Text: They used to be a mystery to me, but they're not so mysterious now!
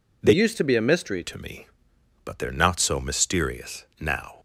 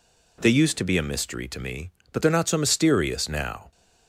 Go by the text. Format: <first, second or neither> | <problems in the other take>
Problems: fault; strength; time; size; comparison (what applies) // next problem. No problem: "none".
second | changes voice from "used" to "mystery"; from 0.3 to 1.2 s; 0.9 s long